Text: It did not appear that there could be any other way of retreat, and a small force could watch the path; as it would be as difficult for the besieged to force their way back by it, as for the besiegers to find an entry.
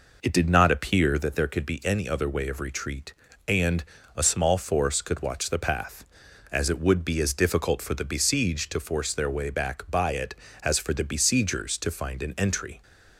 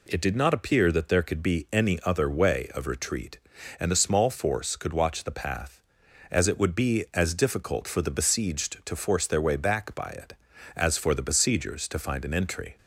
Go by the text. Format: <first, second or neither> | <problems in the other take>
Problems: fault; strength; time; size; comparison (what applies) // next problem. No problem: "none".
second | starts louder than the rest; noticeable; until 1.3 s; 4.5 dB // pauses between "and" and "a"; slight; at 3.8 s; 0.32 s long